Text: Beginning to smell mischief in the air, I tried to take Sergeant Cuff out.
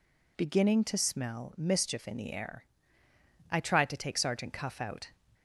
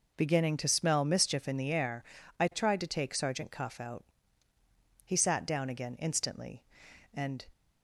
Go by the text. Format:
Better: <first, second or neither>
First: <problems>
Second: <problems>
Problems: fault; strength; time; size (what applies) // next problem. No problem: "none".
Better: first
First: none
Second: goes on to say "He sat down again instantly and"; strong; from 5.0 s on; 2.4 s long